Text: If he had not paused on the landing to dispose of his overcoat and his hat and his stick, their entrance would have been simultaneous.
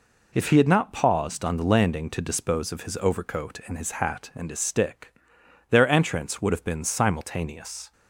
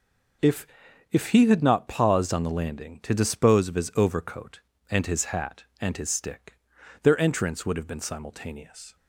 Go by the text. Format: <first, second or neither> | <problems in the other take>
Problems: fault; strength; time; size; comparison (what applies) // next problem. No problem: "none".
first | says "If" twice; at 1.1 s